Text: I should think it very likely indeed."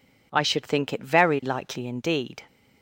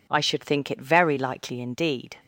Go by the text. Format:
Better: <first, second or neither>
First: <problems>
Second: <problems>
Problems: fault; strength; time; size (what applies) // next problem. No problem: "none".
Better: neither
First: none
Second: none